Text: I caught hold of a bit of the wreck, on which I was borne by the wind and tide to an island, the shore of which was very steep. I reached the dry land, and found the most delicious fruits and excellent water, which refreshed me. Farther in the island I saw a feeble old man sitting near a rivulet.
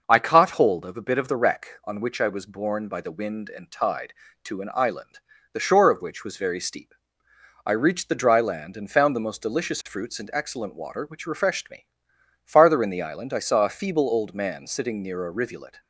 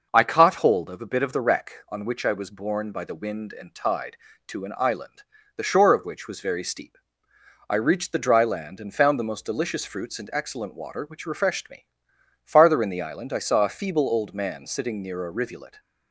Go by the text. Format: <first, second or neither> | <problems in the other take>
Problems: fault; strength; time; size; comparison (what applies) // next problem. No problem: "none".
neither | none